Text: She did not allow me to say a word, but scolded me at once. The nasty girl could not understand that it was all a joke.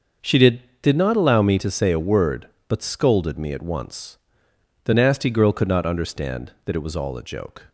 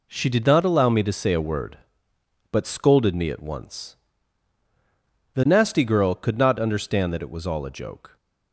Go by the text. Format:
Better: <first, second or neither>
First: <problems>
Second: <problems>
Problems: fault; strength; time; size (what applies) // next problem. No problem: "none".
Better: second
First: starts louder than the rest; until 1.4 s; 6.5 dB // says "did" twice; at 0.8 s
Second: none